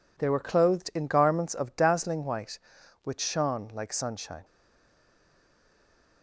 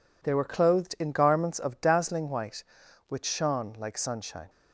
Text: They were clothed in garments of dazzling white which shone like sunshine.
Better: second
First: stays silent after the last word; noticeable; from 4.4 s on; 1.8 s long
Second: none

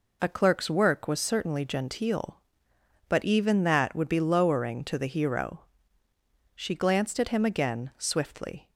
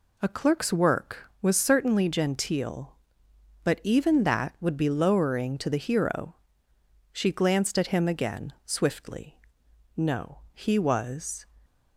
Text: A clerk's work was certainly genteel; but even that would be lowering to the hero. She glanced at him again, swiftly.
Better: first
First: none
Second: goes on to say "No he was"; from 9.9 s on; 1.5 s long

